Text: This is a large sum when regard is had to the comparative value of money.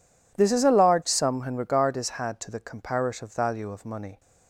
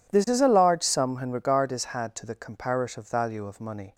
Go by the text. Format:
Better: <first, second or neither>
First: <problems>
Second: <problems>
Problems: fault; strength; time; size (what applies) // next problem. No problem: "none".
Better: neither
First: none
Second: none